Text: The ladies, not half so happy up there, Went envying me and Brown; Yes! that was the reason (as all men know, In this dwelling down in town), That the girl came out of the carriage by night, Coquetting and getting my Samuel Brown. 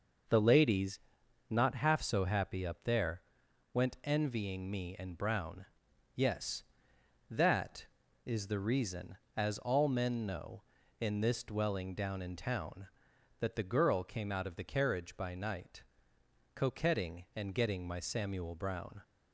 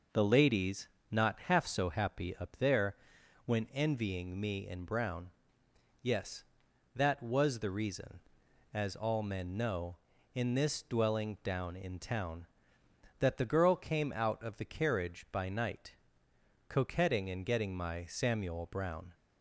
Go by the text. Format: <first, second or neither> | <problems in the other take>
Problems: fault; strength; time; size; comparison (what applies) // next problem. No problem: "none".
second | says "is" for "was"; at 8.2 s